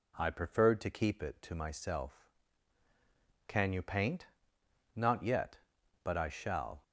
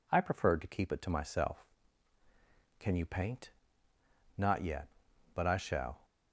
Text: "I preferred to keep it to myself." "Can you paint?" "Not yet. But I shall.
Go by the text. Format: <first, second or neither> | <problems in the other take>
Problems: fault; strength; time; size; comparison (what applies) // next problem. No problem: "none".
neither | none